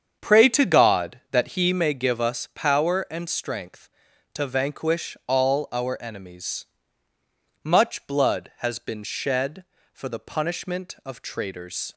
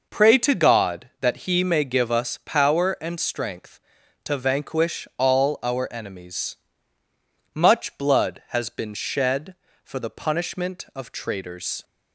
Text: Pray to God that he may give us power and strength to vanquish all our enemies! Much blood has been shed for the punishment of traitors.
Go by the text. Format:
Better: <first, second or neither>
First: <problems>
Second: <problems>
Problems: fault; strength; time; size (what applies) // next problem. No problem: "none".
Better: second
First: starts louder than the rest; strong; until 1.9 s; 7.5 dB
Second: none